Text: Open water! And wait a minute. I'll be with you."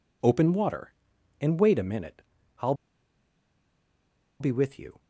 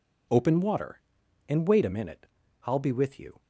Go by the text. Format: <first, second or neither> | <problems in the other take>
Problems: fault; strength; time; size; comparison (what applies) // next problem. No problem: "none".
second | pauses between "I'll" and "be"; strong; at 2.7 s; 1.6 s long